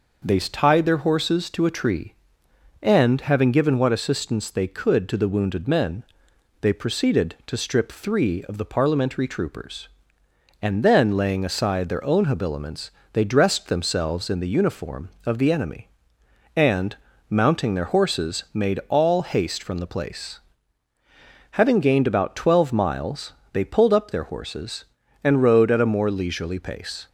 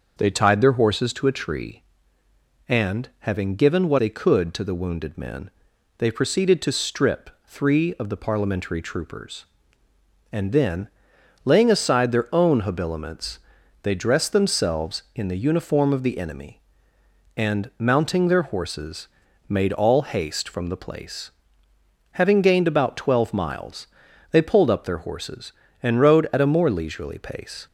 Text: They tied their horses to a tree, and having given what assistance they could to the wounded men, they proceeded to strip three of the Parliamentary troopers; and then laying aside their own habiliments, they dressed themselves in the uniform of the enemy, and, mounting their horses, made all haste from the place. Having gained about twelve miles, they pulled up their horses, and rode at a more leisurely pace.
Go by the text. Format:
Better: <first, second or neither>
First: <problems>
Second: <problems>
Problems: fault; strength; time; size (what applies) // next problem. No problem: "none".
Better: first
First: none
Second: starts louder than the rest; noticeable; until 1.1 s; 6 dB // skips "assistance"; at 3.9 s // pauses between "strip" and "three"; slight; at 7.2 s; 0.18 s long // pauses between "then" and "laying"; noticeable; at 10.8 s; 0.56 s long